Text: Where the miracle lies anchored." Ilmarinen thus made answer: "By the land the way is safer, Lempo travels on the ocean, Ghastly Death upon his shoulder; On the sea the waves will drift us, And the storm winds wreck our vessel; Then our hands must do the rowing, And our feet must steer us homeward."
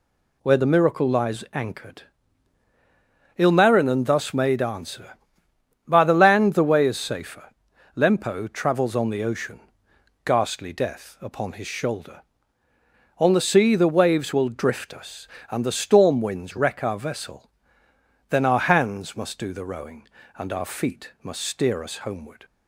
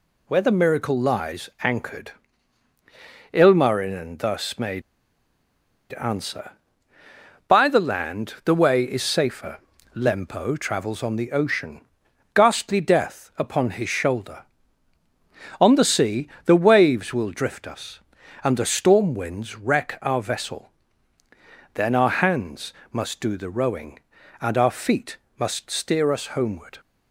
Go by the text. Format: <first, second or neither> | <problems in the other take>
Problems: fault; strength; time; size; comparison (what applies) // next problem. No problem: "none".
first | pauses between "made" and "answer"; at 4.8 s; 1.1 s long // pauses between "sea" and "the"; slight; at 16.2 s; 0.20 s long // pauses between "hands" and "must"; slight; at 22.7 s; 0.18 s long // pauses between "feet" and "must"; slight; at 25.1 s; 0.22 s long